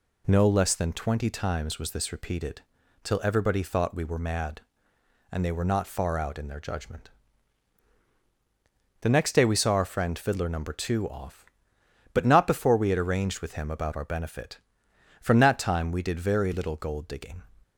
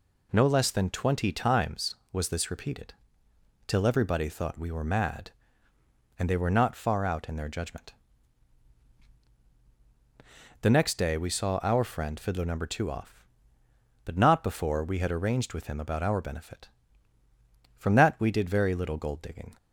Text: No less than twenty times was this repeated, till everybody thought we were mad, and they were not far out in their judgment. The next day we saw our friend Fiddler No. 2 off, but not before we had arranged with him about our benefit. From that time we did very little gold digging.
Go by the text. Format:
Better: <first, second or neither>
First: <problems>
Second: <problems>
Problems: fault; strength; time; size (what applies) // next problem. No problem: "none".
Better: first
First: none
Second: skips "time"; at 18.1 s